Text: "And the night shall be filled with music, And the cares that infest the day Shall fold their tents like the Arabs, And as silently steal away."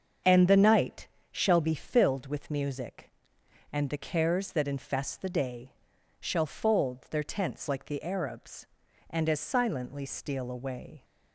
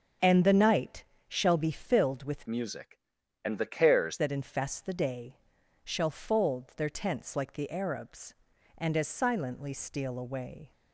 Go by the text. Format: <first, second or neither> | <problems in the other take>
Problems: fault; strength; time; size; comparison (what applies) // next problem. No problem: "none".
first | starts louder than the rest; until 1.4 s; 6.5 dB; also in the first // pauses between "night" and "shall"; slight; at 1.0 s; 0.26 s long; slight in the first // changes voice from "music" to "cares"; from 2.4 to 4.1 s; 1.7 s long // pauses between "day" and "Shall"; noticeable; at 5.3 s; 0.48 s long; noticeable in the first